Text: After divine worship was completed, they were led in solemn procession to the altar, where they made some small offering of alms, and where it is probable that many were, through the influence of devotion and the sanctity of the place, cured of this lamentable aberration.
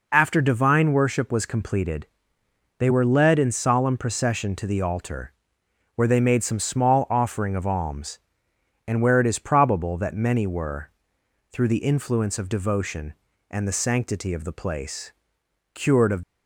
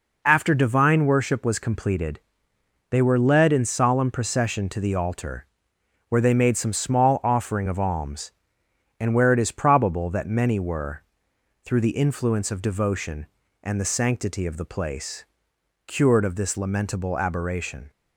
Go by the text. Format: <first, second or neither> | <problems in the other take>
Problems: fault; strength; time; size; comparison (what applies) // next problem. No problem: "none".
second | stops before "this lamentable aberration"; at 16.2 s